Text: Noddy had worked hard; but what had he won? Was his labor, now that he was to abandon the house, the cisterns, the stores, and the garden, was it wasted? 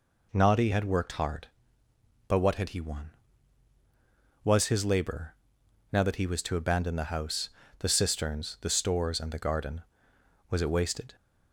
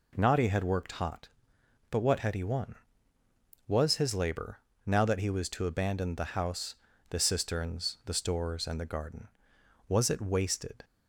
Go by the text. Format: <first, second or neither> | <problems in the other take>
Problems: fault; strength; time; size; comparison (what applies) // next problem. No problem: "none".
first | says "hot" for "hard"; at 0.9 s